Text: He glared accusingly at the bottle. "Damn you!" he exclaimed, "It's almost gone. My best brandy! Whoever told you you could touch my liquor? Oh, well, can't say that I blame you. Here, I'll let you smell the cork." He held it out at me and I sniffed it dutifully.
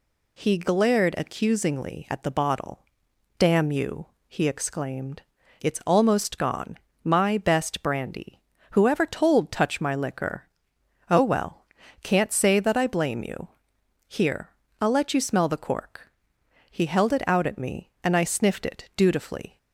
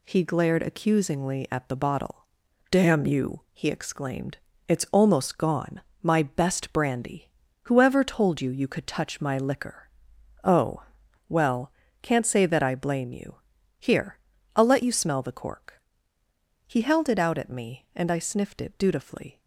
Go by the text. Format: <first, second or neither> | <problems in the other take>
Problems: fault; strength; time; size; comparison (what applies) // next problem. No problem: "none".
second | skips "you you could"; at 9.4 s